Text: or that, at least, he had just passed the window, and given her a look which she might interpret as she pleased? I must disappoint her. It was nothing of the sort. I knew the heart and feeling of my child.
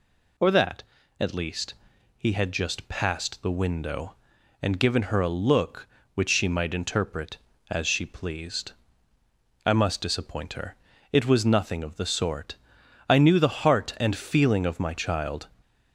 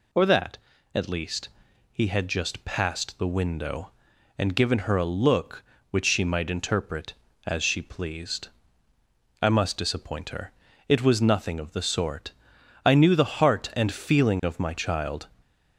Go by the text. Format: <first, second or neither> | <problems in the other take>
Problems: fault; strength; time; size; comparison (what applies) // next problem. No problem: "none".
neither | none